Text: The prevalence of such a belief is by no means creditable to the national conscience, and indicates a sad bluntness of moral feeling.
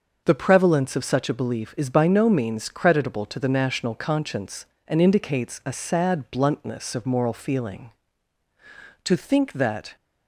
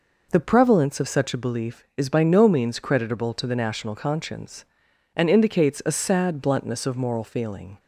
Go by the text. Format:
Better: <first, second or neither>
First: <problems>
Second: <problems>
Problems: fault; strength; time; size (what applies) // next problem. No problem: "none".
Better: second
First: starts louder than the rest; noticeable; until 1.2 s; 6 dB // goes on to say "To think that"; noticeable; from 9.0 s on; 0.90 s long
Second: none